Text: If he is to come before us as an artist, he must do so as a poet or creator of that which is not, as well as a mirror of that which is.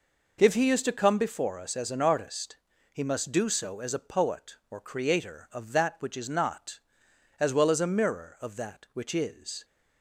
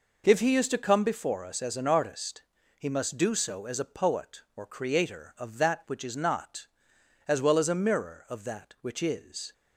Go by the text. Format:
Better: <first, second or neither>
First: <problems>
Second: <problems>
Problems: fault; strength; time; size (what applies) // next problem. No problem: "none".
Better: neither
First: none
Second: none